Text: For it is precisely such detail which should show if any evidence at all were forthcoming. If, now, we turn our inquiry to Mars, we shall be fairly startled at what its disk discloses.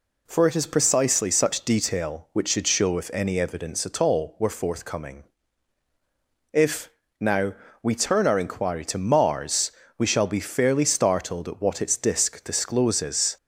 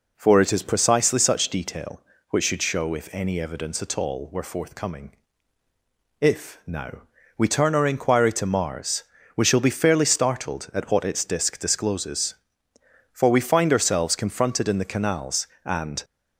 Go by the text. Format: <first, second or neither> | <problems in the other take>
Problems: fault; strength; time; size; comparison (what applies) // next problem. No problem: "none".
first | goes on to say "For we find ourselves confronted in the canals and"; strong; from 13.1 s on; 2.9 s long